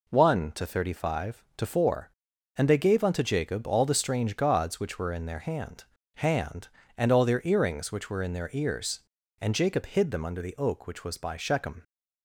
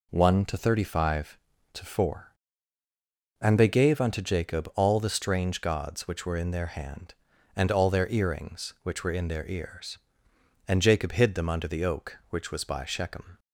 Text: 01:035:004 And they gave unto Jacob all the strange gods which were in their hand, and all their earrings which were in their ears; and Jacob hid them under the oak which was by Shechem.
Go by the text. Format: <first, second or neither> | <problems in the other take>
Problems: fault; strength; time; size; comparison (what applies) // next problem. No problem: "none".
second | says "hand" twice; at 6.1 s